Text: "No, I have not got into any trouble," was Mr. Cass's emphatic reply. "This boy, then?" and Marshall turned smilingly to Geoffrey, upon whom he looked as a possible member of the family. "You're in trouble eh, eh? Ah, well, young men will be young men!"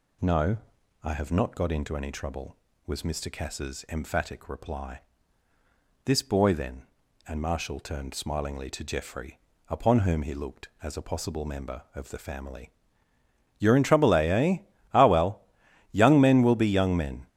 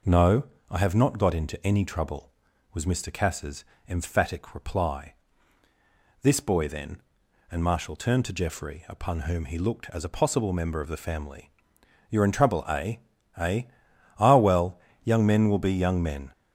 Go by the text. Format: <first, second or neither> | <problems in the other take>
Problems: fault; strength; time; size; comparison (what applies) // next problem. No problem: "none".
first | pauses between "Cass's" and "emphatic"; slight; at 3.6 s; 0.22 s long // skips "smilingly"; at 8.2 s